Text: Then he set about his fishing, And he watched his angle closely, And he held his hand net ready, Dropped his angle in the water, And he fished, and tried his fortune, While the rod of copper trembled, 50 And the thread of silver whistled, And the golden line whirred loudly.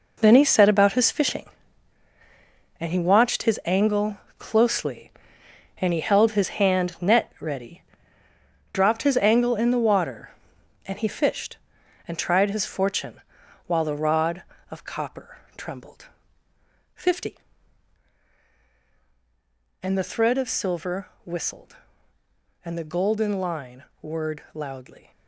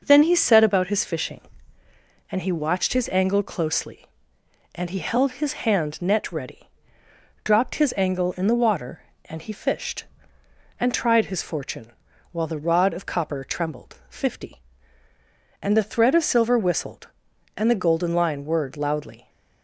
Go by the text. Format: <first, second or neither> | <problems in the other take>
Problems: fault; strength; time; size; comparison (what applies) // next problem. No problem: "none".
second | gets quieter; strong; throughout; 10.5 dB // pauses between "angle" and "closely"; slight; at 4.1 s; 0.22 s long // pauses between "copper" and "trembled"; slight; at 15.3 s; 0.18 s long // pauses between "silver" and "whistled"; slight; at 21.0 s; 0.16 s long // pauses between "line" and "whirred"; slight; at 23.8 s; 0.18 s long